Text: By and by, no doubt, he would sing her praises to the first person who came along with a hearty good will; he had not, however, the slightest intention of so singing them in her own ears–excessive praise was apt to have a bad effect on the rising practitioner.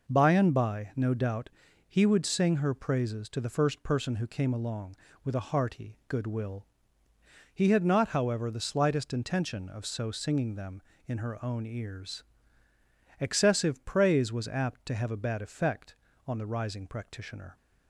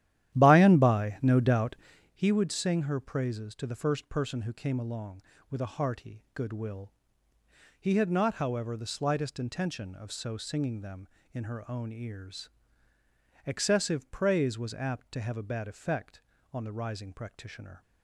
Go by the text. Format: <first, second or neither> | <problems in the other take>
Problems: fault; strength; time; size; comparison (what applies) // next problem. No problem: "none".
first | starts louder than the rest; strong; until 2.2 s; 12 dB